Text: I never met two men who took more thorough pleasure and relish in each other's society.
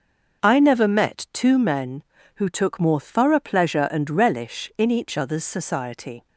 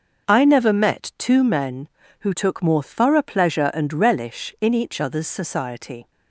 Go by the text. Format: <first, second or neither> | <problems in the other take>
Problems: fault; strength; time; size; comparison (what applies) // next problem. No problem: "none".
neither | starts louder than the rest; the same in both